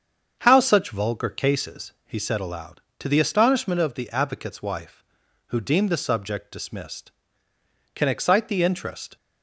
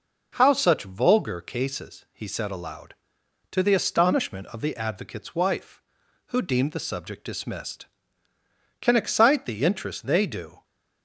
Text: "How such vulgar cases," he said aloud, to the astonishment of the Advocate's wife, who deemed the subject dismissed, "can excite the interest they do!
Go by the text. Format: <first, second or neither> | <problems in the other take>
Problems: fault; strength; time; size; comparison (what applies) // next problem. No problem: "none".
second | starts louder than the rest; until 1.4 s; 7 dB // stops before "they do"; at 9.1 s